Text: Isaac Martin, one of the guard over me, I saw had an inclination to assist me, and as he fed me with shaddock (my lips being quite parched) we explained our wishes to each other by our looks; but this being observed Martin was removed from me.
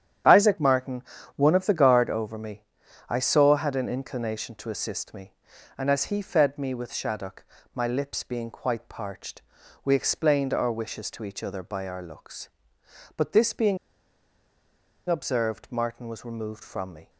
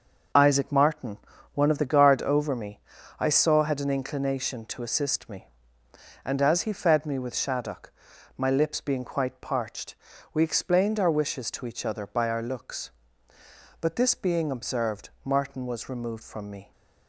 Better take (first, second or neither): second